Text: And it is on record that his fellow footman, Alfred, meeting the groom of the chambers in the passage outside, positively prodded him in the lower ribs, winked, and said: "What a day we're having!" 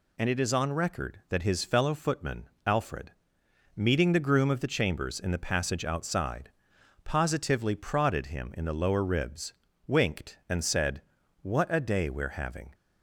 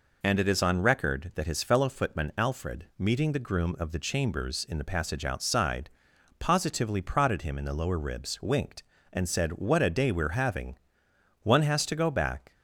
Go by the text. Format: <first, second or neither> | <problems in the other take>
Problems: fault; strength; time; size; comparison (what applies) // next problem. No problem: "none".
first | goes on to say "One has to go back"; noticeable; from 11.4 s on; 1.1 s long